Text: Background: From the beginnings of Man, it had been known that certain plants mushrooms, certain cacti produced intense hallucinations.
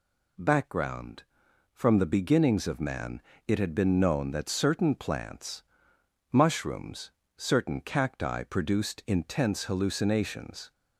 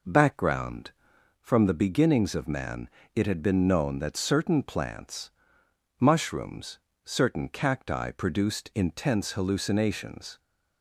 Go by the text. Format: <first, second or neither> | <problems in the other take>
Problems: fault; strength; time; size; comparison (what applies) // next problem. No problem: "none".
first | starts louder than the rest; noticeable; until 1.4 s; 4.5 dB // pauses between "plants" and "mushrooms"; noticeable; at 5.3 s; 0.66 s long; noticeable in the first